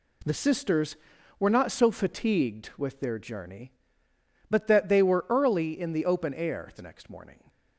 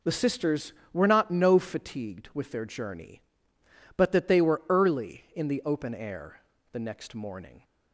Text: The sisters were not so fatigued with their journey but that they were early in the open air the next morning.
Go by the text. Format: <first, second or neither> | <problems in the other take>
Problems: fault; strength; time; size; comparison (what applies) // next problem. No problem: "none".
first | says "no" for "so"; at 1.3 s // pauses between "air" and "the"; slight; at 6.3 s; 0.32 s long